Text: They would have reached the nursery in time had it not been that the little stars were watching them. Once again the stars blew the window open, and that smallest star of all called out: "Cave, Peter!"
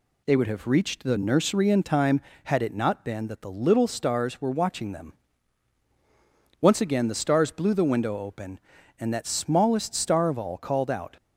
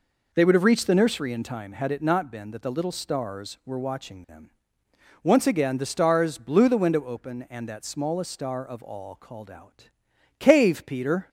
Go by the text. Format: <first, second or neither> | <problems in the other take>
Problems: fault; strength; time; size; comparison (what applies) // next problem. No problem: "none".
second | stops before "Cave Peter"; at 11.1 s